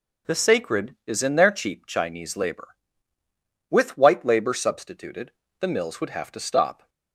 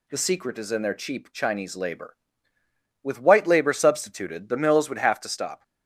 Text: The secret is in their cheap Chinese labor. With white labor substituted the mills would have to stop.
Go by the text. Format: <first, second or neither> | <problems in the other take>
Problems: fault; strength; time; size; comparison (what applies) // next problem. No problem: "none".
second | says "sacred" for "secret"; at 0.3 s // pauses between "substituted" and "the"; slight; at 5.3 s; 0.30 s long